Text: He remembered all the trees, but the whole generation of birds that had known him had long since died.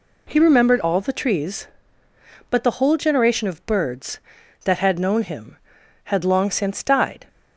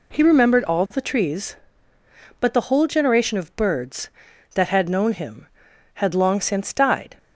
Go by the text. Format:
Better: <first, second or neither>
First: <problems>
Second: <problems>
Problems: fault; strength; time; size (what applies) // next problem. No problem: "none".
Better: neither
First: none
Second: none